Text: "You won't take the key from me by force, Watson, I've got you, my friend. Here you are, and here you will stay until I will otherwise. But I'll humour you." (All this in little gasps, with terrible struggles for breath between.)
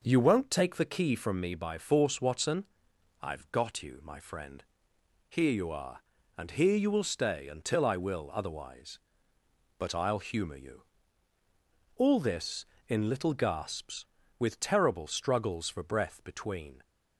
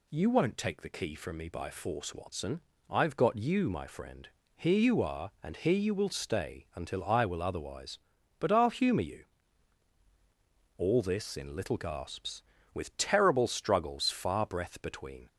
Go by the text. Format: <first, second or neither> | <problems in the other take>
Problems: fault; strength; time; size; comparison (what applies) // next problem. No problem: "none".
first | says "far" for "for"; at 14.0 s